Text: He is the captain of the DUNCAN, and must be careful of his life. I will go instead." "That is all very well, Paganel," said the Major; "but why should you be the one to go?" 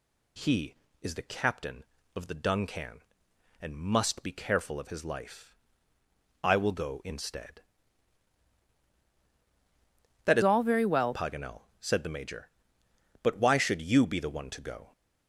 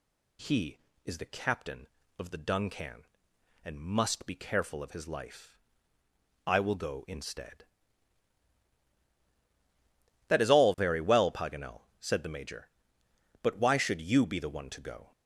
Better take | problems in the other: second | changes voice from "all" to "well"; from 10.4 to 11.1 s; 0.7 s long

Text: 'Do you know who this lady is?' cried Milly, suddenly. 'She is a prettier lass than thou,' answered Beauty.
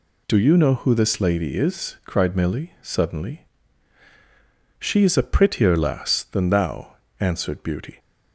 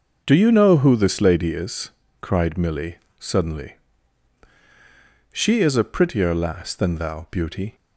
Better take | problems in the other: first | skips "answered"; at 7.2 s

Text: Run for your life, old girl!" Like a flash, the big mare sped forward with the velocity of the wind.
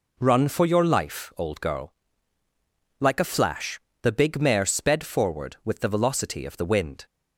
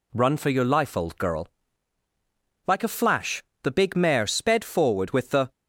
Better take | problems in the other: first | stops before "velocity of the wind"; at 5.5 s

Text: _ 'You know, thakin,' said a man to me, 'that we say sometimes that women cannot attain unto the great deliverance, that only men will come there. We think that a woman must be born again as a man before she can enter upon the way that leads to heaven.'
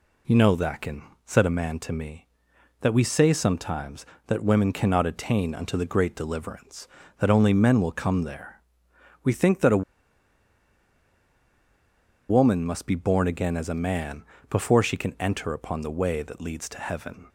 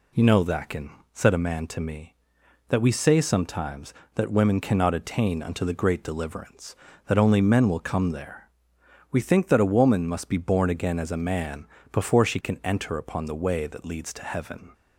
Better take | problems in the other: second | pauses between "a" and "woman"; strong; at 9.8 s; 2.4 s long // pauses between "man" and "before"; slight; at 14.2 s; 0.26 s long; slight in the second

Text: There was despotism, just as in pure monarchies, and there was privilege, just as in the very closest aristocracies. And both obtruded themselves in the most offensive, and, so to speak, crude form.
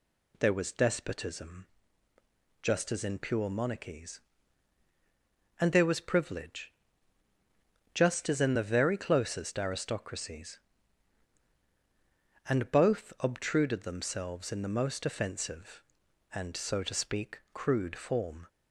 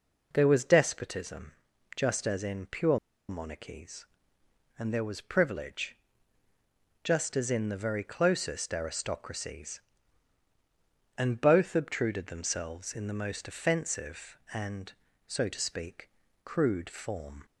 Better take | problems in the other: first | pauses between "pure" and "monarchies"; slight; at 2.9 s; 0.32 s long

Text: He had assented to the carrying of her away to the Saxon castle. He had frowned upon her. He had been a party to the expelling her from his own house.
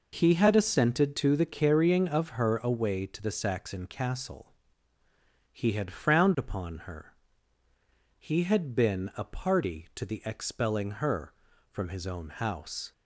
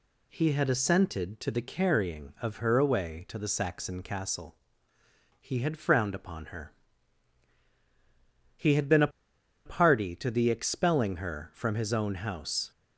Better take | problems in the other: first | pauses between "a" and "party"; noticeable; at 9.0 s; 0.56 s long

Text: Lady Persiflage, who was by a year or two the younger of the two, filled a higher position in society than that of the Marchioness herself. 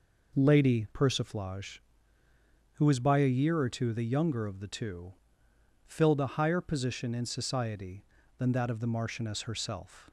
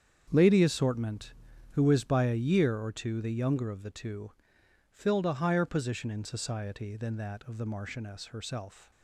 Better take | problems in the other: first | starts louder than the rest; strong; until 1.3 s; 8 dB // says "Assortment" for "Persiflage"; at 0.6 s

